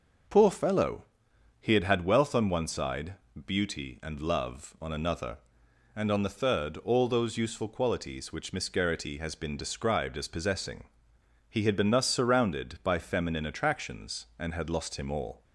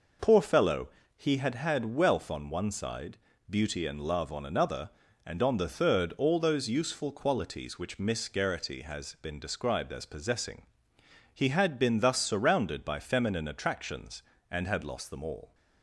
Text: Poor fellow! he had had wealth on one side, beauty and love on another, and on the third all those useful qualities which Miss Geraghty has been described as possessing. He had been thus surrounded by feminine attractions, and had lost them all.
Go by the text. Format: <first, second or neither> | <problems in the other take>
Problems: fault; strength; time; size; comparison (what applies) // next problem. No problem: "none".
second | says "him" for "them"; at 14.9 s